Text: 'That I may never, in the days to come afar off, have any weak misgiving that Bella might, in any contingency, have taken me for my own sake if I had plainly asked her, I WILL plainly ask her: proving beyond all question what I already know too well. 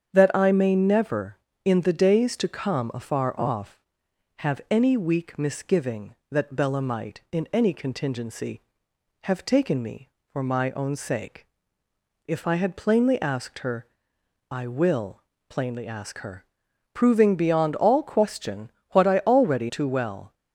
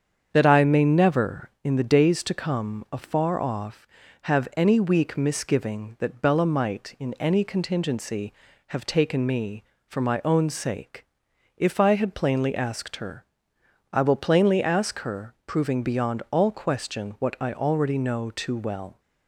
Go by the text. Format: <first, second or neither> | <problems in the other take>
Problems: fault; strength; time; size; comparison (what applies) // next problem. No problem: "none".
second | starts louder than the rest; strong; until 1.1 s; 8 dB; strong in the second // pauses between "sake" and "if"; noticeable; at 11.4 s; 0.82 s long; noticeable in the second // pauses between "WILL" and "plainly"; slight; at 15.1 s; 0.30 s long // pauses between "question" and "what"; slight; at 18.7 s; 0.22 s long // skips "know"; at 19.6 s